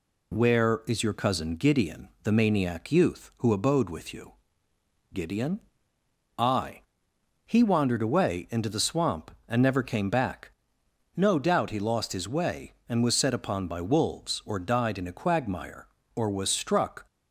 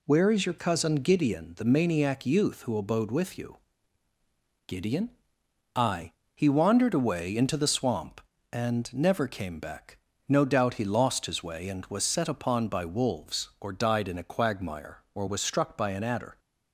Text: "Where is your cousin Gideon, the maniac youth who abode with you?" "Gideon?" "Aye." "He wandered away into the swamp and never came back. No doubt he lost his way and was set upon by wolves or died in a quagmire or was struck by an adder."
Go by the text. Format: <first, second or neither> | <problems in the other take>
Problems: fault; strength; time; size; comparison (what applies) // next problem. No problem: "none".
second | stops before "by an adder"; at 17.0 s